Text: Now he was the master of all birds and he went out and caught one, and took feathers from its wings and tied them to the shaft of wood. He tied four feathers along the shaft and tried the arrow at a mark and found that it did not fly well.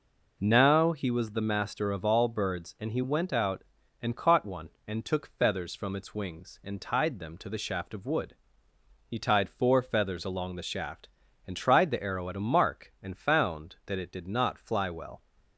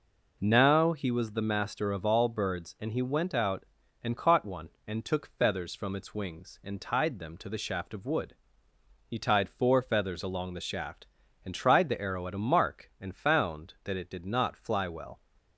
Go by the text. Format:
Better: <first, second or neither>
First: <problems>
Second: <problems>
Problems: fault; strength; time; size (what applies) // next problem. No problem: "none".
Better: neither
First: none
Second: none